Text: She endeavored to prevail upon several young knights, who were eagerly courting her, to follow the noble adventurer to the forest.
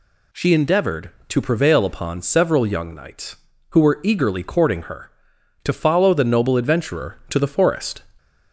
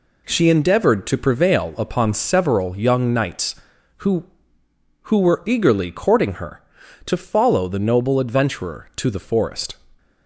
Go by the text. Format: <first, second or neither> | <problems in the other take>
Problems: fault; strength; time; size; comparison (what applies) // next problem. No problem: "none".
first | says "who" twice; at 5.0 s